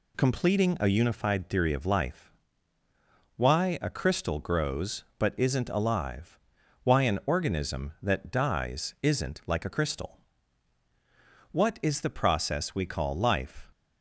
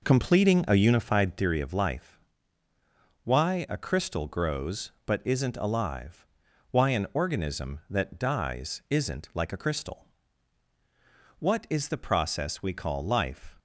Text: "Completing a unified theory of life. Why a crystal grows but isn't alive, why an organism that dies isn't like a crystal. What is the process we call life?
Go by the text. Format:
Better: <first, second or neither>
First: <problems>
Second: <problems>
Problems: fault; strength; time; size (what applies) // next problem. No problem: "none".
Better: first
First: none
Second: starts louder than the rest; noticeable; until 1.5 s; 5 dB